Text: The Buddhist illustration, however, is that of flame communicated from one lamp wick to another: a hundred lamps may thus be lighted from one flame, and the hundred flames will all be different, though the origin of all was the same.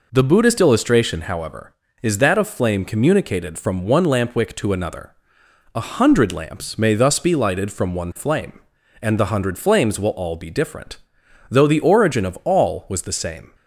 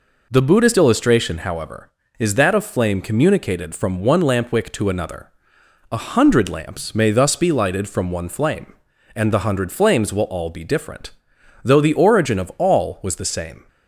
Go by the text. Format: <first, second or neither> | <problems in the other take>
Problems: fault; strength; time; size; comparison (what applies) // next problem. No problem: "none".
neither | none